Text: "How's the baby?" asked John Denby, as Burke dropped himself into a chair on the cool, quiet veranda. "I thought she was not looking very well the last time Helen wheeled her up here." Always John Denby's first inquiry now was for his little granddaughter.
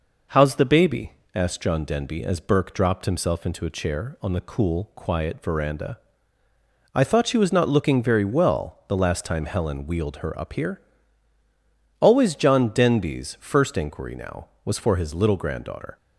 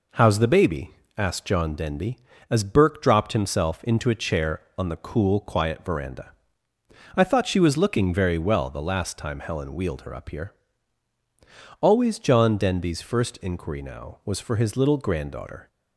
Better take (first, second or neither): first